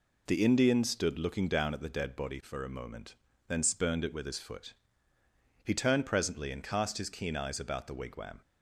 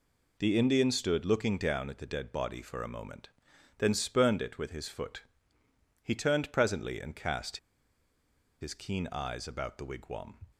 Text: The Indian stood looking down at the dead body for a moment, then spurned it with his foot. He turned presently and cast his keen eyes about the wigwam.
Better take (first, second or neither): first